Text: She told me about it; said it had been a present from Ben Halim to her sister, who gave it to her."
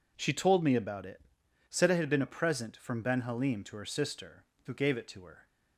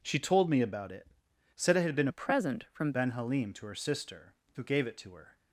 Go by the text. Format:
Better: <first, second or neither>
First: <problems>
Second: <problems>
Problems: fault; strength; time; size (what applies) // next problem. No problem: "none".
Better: first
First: none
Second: changes voice from "a" to "from"; from 2.1 to 2.9 s; 0.8 s long